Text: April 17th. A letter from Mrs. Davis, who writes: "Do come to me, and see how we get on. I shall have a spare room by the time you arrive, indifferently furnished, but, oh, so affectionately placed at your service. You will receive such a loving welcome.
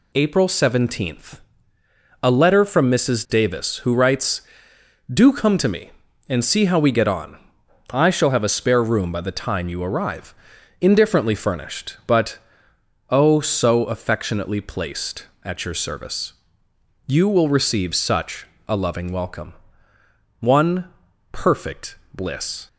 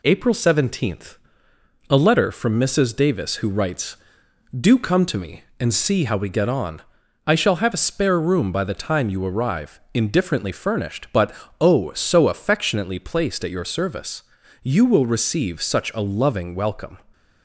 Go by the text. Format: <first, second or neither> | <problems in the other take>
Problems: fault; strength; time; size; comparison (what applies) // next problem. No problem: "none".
second | pauses between "such" and "a"; slight; at 18.4 s; 0.22 s long // goes on to say "One perfect bliss"; strong; from 20.3 s on; 2.2 s long